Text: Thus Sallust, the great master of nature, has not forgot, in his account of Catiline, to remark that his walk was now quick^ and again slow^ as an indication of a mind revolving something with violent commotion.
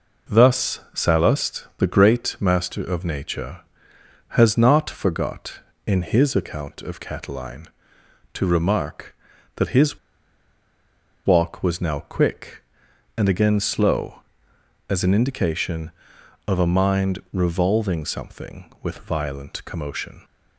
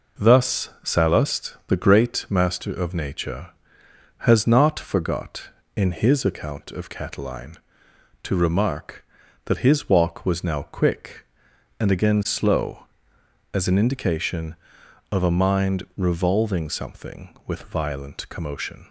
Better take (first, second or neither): second